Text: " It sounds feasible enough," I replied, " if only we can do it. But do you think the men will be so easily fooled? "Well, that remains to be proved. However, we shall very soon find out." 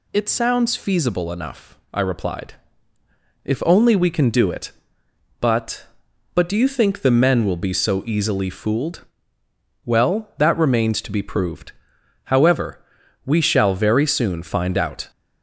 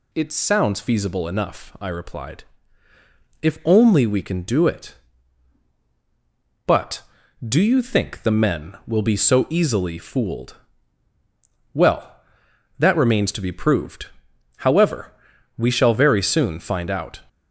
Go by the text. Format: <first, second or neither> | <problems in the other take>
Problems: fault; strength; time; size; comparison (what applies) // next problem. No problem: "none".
second | says "But" twice; at 6.3 s